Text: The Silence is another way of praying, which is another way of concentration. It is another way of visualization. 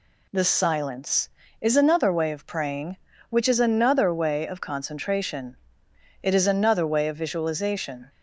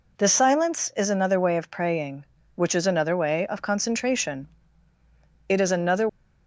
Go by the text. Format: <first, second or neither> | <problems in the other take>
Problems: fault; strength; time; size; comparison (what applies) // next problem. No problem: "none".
first | stops before "way of visualization"; at 6.0 s